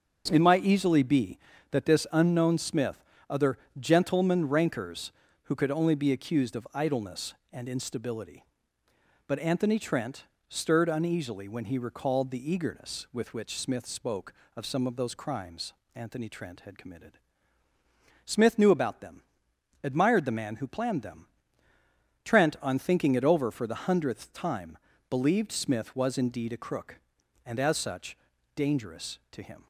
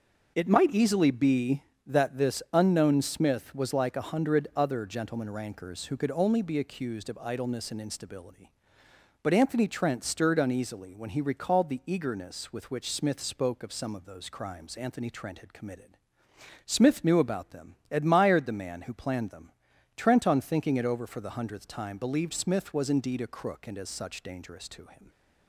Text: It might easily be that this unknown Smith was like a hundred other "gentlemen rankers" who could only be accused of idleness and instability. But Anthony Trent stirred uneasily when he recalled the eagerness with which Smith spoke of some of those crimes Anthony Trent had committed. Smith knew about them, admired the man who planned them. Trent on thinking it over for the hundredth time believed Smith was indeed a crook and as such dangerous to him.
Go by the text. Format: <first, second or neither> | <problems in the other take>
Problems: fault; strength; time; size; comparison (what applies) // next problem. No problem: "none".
second | starts louder than the rest; until 1.3 s; 6.5 dB; noticeable in the second // skips "was like a hundred"; at 3.1 s // pauses between "other" and "gentlemen"; slight; at 3.5 s; 0.20 s long // pauses between "Trent" and "stirred"; slight; at 10.2 s; 0.24 s long // pauses between "crimes" and "Anthony"; slight; at 15.7 s; 0.20 s long // pauses between "time" and "believed"; slight; at 24.7 s; 0.32 s long // pauses between "such" and "dangerous"; at 28.1 s; 0.38 s long